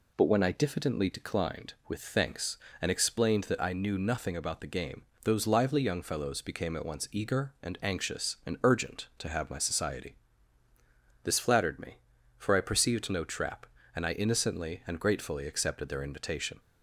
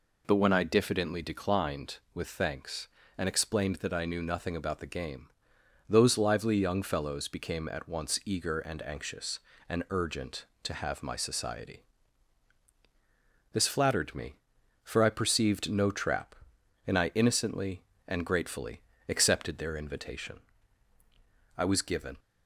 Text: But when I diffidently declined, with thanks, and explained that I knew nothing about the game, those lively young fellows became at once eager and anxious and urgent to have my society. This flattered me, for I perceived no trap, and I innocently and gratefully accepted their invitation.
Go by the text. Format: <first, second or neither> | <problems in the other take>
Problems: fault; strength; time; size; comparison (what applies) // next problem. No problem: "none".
first | pauses between "gratefully" and "accepted"; slight; at 18.7 s; 0.28 s long // goes on to say "I was given"; noticeable; from 21.5 s on; 0.62 s long